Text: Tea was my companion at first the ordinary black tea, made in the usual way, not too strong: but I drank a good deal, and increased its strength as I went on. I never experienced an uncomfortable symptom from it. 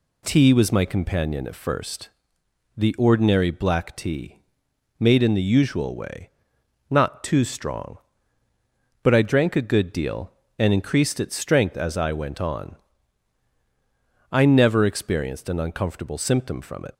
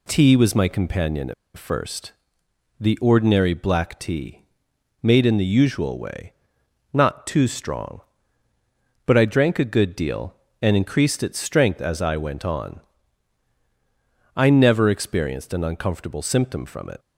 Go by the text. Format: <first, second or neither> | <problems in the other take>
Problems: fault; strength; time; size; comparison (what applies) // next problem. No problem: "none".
first | pauses between "at" and "first"; slight; at 1.3 s; 0.23 s long // pauses between "first" and "the"; noticeable; at 2.1 s; 0.68 s long; noticeable in the first